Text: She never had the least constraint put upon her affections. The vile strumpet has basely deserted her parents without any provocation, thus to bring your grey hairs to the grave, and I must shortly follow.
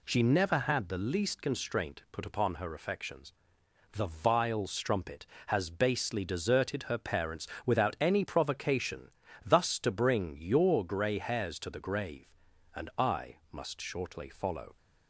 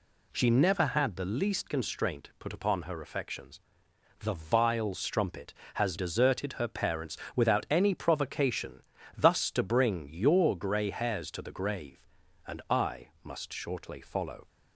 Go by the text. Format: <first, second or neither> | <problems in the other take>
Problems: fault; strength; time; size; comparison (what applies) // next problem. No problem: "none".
first | skips "basely"; at 5.9 s // pauses between "parents" and "without"; slight; at 7.1 s; 0.20 s long; slight in the first